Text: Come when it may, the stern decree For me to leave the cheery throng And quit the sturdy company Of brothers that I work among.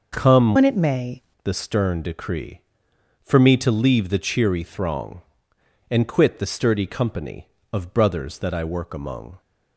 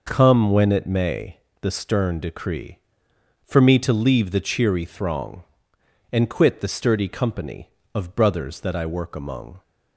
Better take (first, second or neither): second